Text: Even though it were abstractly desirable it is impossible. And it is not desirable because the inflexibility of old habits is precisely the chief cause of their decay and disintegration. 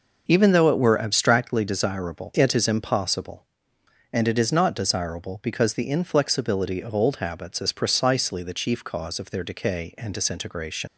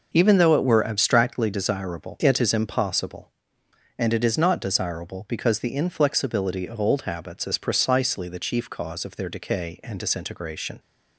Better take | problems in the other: second | leaves "disintegration" unfinished; at 10.8 s; 65 ms

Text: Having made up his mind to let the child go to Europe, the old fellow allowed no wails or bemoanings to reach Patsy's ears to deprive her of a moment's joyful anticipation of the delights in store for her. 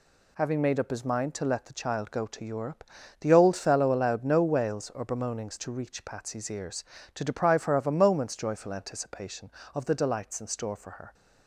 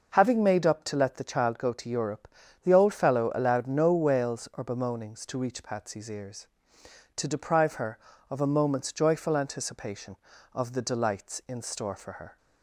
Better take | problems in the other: first | skips "his mind"; at 0.8 s

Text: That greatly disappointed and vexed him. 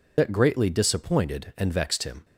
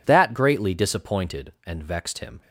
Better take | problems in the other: second | loses the start of "That"; at 0.1 s; 55 ms

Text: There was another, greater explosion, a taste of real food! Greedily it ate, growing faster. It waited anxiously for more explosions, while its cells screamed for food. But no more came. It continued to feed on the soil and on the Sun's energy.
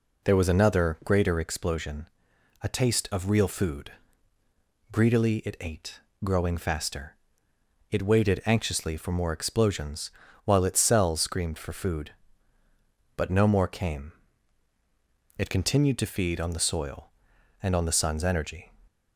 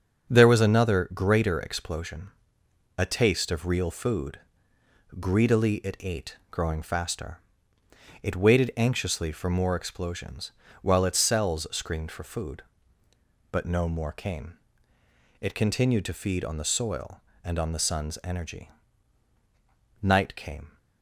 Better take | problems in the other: first | starts louder than the rest; until 1.3 s; 7 dB // goes on to say "Night came"; noticeable; from 20.0 s on; 0.76 s long

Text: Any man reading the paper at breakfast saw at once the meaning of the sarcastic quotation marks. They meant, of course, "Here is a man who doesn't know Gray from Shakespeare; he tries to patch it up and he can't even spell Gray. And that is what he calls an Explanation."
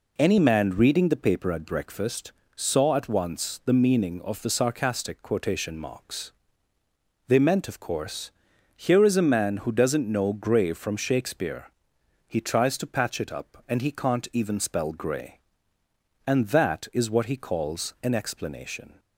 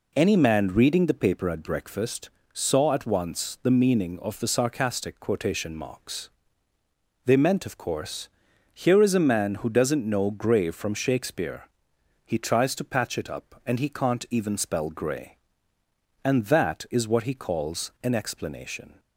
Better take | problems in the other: neither | pauses between "breakfast" and "saw"; slight; the same in both

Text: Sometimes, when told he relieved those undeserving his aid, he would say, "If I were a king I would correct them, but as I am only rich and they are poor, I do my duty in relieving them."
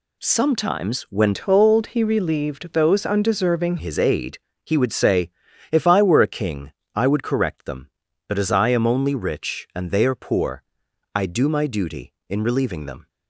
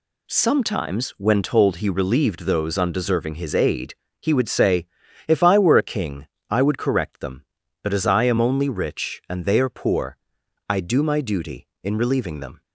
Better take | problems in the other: second | changes voice from "told" to "undeserving"; from 1.3 to 3.7 s; 2.4 s long // pauses between "king" and "I"; slight; at 6.6 s; 0.24 s long; slight in the second

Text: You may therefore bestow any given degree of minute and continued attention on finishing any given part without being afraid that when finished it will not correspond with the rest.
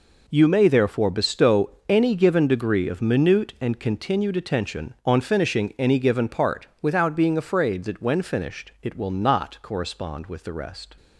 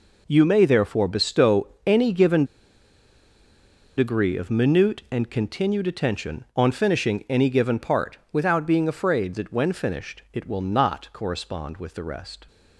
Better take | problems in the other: first | pauses between "bestow" and "any"; slight; at 1.6 s; 0.20 s long; slight in the first // pauses between "given" and "degree"; strong; at 2.4 s; 1.5 s long

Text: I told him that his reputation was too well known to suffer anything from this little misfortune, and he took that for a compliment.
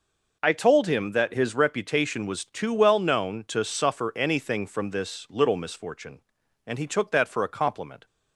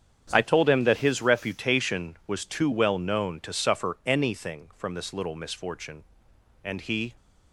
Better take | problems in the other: first | starts louder than the rest; strong; until 1.3 s; 8 dB // stops before "took that for a compliment"; at 7.1 s

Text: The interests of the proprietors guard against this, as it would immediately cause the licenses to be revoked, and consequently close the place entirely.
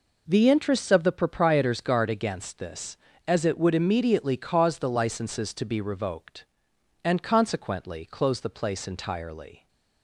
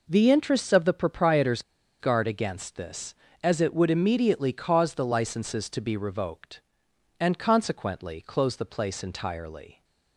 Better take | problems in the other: first | pauses between "proprietors" and "guard"; at 1.6 s; 0.38 s long

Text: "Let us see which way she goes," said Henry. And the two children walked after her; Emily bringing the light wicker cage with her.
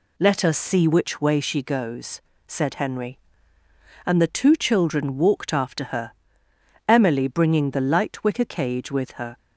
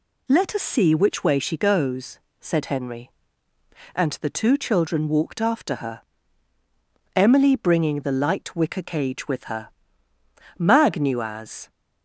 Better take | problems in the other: first | goes on to say "Mag knew as"; noticeable; from 10.5 s on; 1.1 s long

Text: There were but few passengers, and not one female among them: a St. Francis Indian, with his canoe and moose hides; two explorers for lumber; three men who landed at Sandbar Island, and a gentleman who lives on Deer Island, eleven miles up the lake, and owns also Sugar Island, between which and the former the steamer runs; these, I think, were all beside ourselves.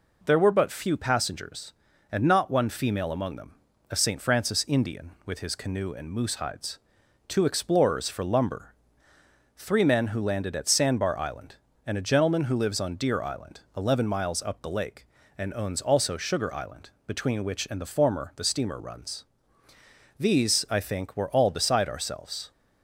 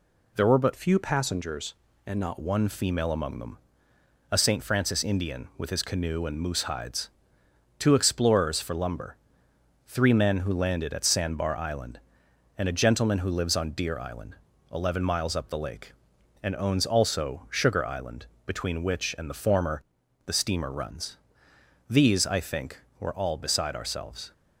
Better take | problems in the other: first | changes voice from "few" to "not"; from 0.7 to 2.3 s; 1.6 s long // pauses between "former" and "the"; noticeable; at 19.8 s; 0.46 s long

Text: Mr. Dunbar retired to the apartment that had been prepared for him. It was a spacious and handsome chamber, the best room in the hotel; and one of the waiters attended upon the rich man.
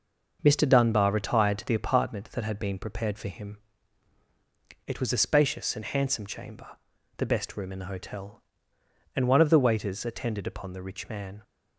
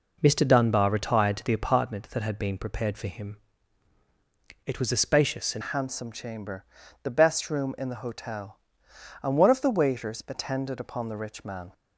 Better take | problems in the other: first | changes voice at "handsome"; from 5.6 s on; 6.1 s long

